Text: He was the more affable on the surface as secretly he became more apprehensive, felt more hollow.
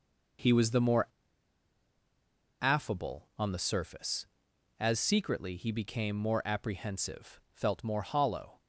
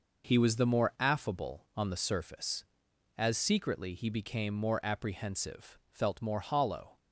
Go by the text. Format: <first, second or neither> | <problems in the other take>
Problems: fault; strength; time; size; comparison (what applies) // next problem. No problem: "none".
second | pauses between "more" and "affable"; strong; at 1.0 s; 1.5 s long